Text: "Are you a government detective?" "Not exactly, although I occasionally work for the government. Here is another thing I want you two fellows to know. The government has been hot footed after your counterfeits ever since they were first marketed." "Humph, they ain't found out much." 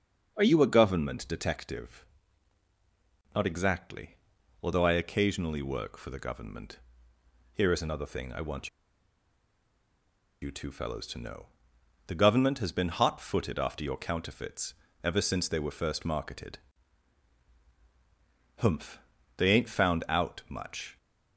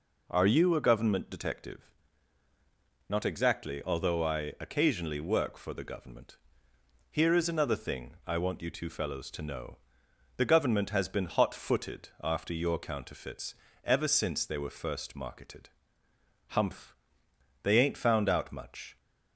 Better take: second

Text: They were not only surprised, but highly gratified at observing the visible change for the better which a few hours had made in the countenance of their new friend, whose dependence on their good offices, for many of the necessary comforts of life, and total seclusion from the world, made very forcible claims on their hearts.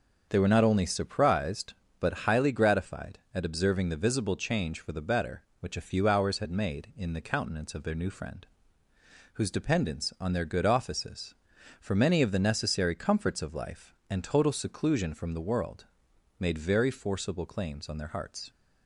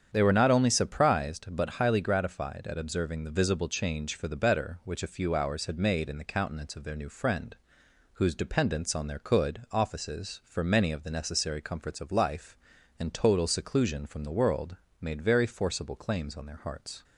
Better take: first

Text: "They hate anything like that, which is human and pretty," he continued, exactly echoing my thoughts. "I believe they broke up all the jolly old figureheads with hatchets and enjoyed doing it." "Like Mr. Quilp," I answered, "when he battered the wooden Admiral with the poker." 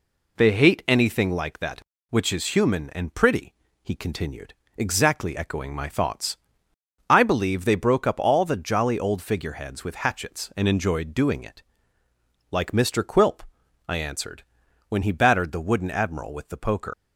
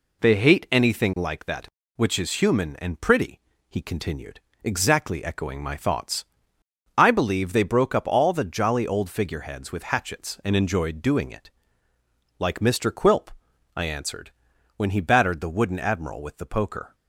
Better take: second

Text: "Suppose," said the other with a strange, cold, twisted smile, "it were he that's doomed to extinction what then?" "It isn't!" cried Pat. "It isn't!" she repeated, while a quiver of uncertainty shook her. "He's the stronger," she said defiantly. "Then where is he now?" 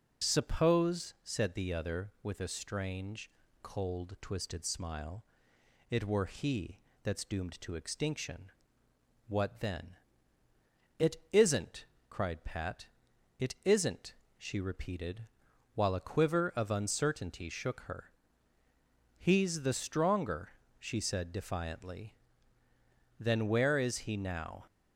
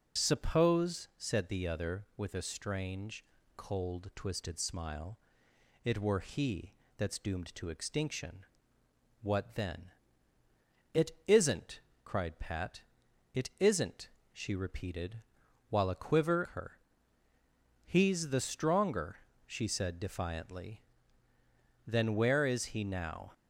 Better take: first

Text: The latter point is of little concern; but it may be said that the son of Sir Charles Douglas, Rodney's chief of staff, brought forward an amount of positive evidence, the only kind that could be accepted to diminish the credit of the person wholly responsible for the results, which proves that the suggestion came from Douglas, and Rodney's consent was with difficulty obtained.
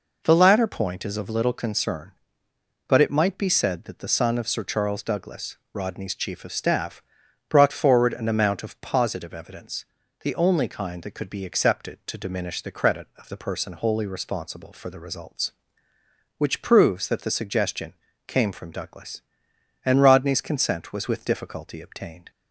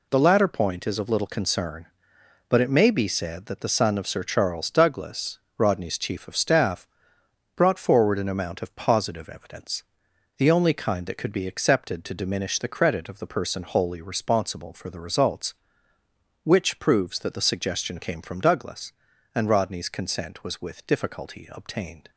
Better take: second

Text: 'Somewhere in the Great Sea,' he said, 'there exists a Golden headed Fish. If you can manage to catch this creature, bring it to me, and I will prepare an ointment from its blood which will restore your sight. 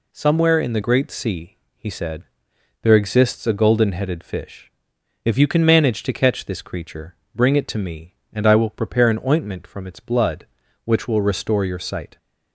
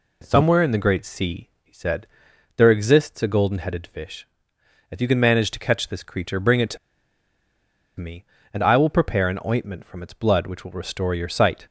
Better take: first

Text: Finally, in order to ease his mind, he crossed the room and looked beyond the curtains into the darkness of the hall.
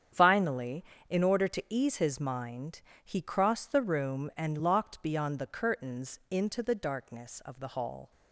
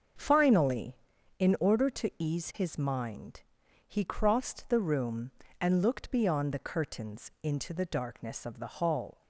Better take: second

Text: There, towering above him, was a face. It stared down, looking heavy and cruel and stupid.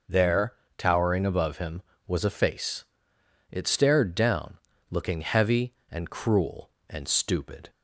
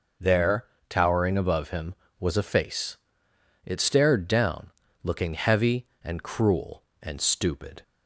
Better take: neither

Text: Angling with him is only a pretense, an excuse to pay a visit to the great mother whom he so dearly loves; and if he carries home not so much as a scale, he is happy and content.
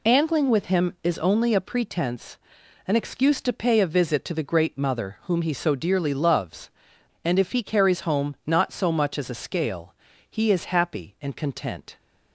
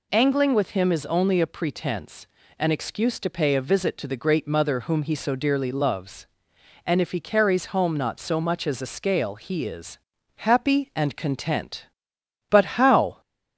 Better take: first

